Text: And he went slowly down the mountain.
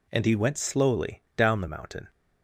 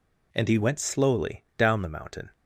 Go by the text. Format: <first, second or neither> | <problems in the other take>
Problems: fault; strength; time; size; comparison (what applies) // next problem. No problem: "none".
neither | none